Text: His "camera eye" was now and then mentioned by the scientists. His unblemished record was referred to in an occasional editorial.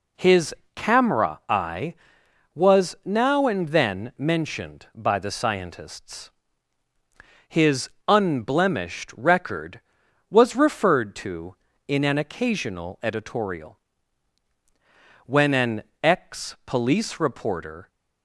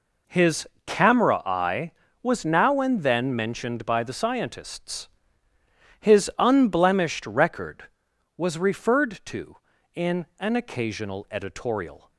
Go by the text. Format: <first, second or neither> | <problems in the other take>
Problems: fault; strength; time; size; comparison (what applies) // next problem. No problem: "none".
second | pauses between "His" and "camera"; slight; at 0.5 s; 0.20 s long; slight in the second // pauses between "His" and "unblemished"; slight; at 7.9 s; 0.18 s long // goes on to say "When an ex police reporter"; strong; from 15.2 s on; 2.6 s long